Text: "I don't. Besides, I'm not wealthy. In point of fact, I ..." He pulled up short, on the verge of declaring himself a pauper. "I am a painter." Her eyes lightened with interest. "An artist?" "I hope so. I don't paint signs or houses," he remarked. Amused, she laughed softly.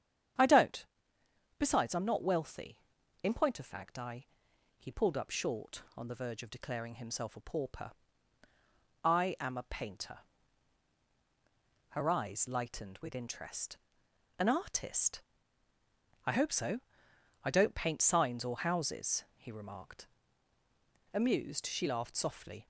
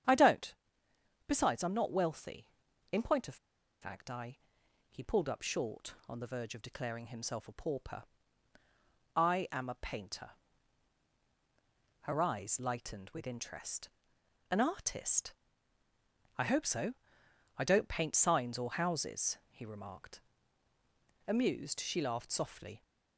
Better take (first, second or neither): first